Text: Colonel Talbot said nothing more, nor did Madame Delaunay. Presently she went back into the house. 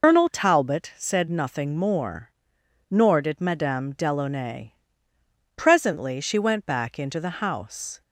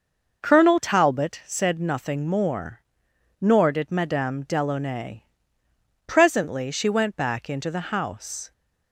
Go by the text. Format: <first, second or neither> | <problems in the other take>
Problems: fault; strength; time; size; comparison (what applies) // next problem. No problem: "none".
second | loses the start of "Colonel"; at 0.0 s; 125 ms